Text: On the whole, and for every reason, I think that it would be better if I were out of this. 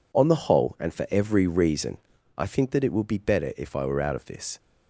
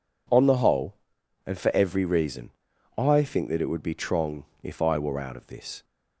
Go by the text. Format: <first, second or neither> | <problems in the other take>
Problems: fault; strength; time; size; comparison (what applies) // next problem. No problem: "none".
first | says "trong" for "better"; at 3.9 s